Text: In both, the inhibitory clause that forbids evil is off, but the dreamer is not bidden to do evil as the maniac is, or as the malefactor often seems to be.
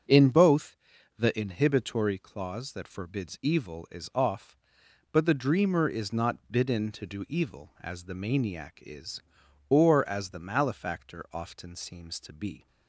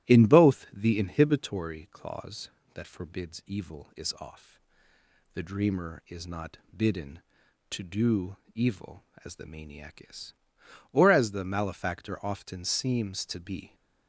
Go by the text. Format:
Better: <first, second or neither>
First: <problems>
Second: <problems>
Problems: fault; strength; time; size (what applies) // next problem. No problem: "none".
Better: first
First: starts louder than the rest; strong; until 1.5 s; 7 dB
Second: starts louder than the rest; strong; until 1.1 s; 14 dB // skips "but"; at 4.9 s // pauses between "not" and "bidden"; slight; at 6.5 s; 0.16 s long // pauses between "do" and "evil"; slight; at 8.3 s; 0.16 s long